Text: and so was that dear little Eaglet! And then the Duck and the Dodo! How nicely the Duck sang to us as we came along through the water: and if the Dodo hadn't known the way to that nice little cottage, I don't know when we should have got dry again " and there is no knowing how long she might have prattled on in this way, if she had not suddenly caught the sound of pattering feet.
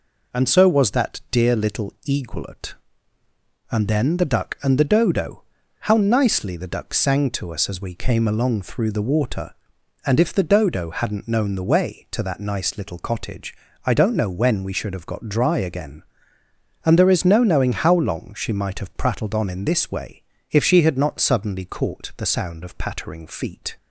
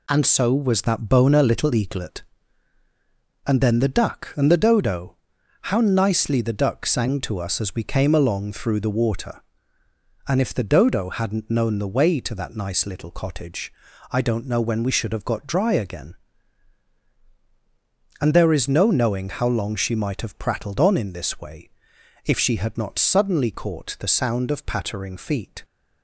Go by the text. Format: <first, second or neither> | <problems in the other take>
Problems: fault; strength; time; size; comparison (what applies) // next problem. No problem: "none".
first | says "boner" for "dear"; at 1.0 s